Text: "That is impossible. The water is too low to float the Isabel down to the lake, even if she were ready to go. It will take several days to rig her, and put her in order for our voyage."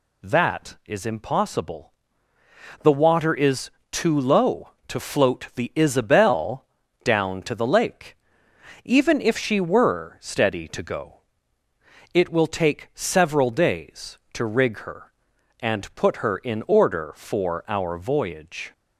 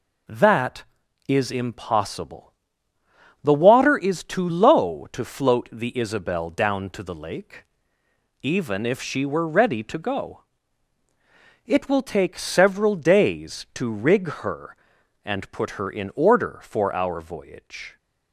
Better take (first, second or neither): second